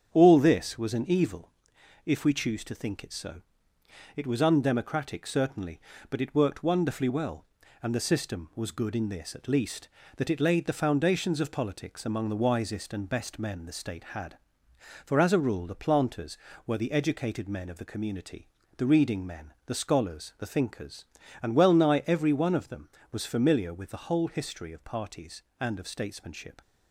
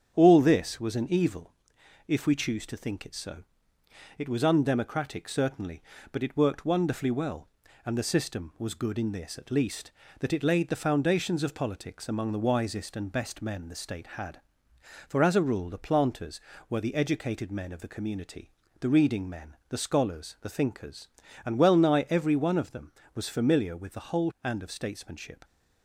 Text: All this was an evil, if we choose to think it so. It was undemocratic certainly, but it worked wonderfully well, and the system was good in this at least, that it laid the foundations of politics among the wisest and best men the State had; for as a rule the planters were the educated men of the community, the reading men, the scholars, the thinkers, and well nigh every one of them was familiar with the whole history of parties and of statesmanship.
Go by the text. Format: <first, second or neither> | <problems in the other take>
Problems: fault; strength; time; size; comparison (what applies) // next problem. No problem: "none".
first | starts louder than the rest; strong; until 1.1 s; 8 dB; strong in the first // skips "history of parties"; at 24.3 s